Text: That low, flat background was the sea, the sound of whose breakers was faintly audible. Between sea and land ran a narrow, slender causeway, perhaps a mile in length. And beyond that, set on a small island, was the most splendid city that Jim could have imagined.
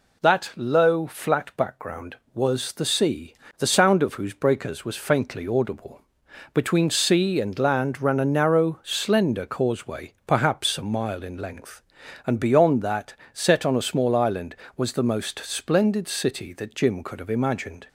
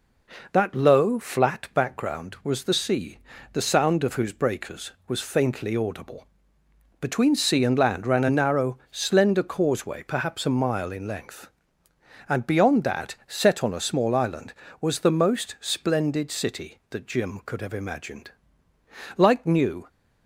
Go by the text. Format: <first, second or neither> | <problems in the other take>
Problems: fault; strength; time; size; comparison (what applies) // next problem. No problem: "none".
first | goes on to say "Like New"; noticeable; from 19.1 s on; 0.70 s long